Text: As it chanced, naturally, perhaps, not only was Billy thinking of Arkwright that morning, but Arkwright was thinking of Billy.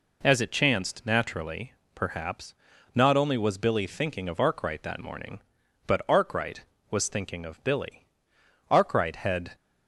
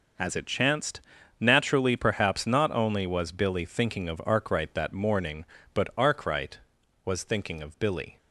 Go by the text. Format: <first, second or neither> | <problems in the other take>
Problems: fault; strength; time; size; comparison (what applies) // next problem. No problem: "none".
second | goes on to say "Arkwright had"; noticeable; from 8.6 s on; 0.86 s long